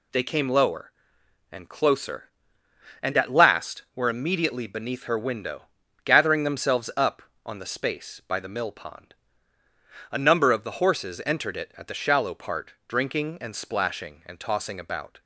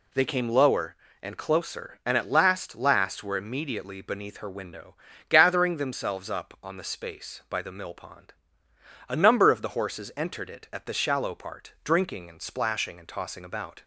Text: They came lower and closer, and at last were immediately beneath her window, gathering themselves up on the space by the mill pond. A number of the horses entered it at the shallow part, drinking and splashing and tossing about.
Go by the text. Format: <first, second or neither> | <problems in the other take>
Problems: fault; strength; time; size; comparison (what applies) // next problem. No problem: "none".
first | says "last" twice; at 2.7 s